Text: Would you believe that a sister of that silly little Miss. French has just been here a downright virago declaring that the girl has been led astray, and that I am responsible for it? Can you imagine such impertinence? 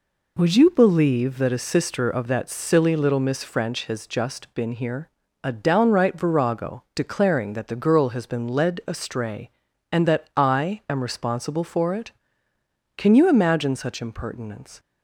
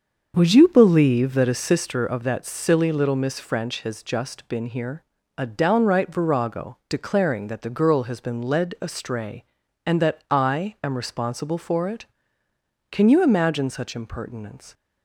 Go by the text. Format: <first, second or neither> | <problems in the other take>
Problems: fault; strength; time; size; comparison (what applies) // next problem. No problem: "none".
first | starts louder than the rest; until 1.8 s; 7 dB // pauses between "here" and "a"; slight; at 5.0 s; 0.34 s long; slight in the first